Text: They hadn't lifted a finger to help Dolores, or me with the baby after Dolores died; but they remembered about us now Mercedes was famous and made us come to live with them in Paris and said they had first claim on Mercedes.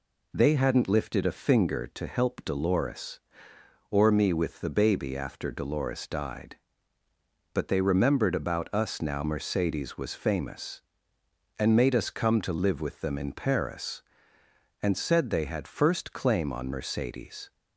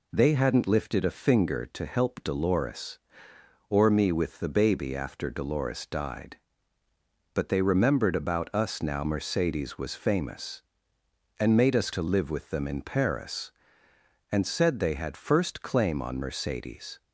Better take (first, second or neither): first